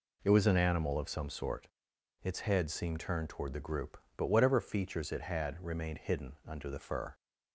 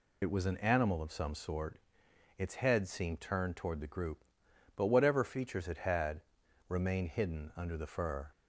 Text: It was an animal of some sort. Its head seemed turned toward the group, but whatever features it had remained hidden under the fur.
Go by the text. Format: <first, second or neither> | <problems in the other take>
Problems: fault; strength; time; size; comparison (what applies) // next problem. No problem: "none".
first | loses the start of "It"; at 0.2 s; 70 ms // pauses between "had" and "remained"; noticeable; at 6.2 s; 0.46 s long